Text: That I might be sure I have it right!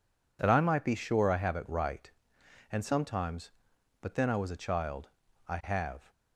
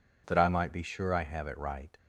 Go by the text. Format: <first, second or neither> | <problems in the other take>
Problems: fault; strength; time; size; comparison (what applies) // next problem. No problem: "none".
second | goes on to say "And sometimes but then I was a child I have"; strong; from 2.7 s on; 3.3 s long